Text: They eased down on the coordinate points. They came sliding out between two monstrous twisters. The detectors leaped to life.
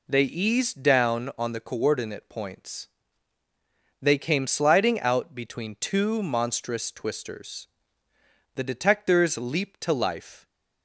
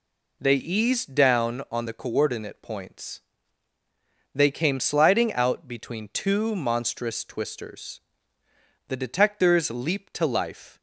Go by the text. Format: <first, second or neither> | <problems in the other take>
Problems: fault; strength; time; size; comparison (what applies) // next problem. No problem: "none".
neither | none